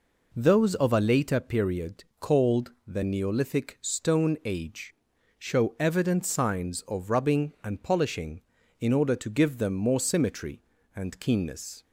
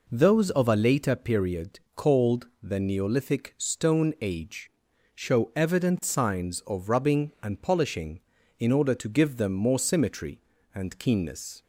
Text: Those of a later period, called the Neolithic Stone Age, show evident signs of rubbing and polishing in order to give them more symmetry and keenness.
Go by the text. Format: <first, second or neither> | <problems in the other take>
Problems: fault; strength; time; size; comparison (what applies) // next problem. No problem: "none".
neither | pauses between "called" and "the"; slight; the same in both